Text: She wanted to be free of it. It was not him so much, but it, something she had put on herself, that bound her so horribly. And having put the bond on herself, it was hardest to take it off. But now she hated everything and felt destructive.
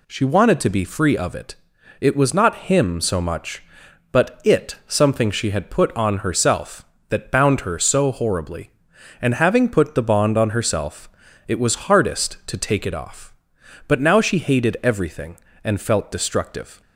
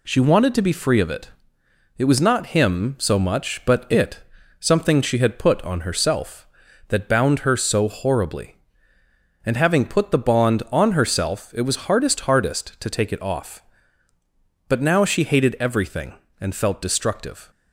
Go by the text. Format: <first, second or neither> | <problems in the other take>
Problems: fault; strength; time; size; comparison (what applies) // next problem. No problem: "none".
first | says "hardest" twice; at 12.2 s